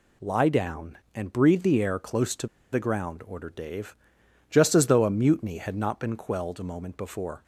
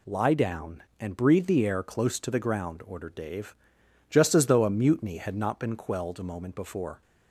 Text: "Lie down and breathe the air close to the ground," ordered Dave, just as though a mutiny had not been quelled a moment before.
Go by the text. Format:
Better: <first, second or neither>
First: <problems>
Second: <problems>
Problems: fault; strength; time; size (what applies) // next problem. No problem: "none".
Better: second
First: pauses between "to" and "the"; slight; at 2.4 s; 0.25 s long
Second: none